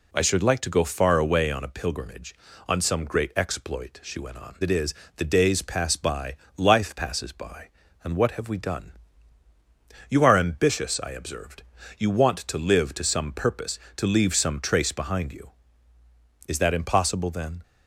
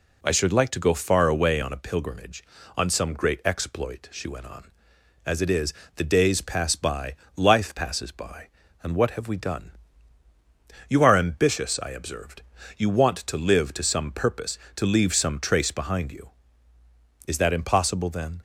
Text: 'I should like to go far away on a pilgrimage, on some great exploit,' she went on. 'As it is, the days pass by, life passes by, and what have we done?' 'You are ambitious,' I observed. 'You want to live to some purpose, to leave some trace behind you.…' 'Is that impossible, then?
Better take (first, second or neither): second